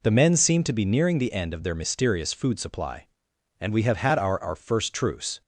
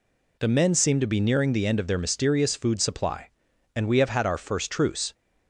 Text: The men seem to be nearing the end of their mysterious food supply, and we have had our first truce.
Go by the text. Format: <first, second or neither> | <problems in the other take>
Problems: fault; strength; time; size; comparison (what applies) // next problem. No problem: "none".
second | says "our" twice; at 4.4 s